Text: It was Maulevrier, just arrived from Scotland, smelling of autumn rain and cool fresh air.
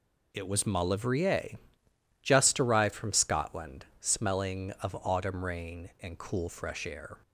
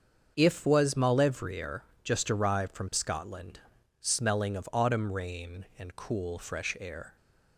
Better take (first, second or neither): first